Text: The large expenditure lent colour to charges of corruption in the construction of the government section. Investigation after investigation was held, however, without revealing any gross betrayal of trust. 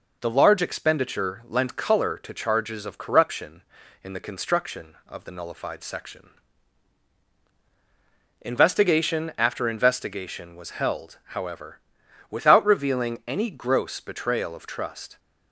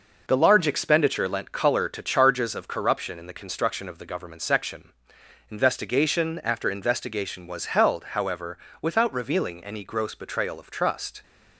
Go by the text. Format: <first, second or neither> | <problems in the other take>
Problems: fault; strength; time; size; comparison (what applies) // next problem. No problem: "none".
second | says "nullified" for "government"; at 5.3 s